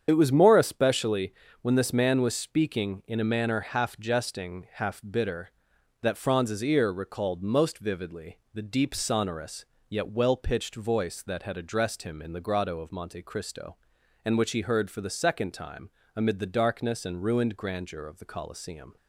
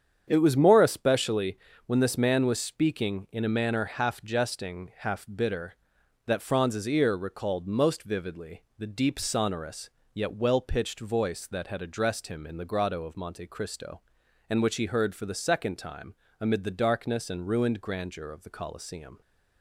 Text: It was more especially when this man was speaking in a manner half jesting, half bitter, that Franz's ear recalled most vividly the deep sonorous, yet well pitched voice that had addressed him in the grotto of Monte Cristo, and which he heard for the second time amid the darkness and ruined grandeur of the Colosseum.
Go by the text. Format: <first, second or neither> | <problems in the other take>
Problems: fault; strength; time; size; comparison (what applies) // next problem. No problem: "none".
second | loses the start of "It"; at 0.0 s; 55 ms // starts louder than the rest; strong; until 1.0 s; 8 dB; strong in the second // pauses between "especially" and "when"; slight; at 1.3 s; 0.30 s long; slight in the second // pauses between "vividly" and "the"; slight; at 8.3 s; 0.16 s long; slight in the second // pauses between "time" and "amid"; slight; at 15.8 s; 0.26 s long; slight in the second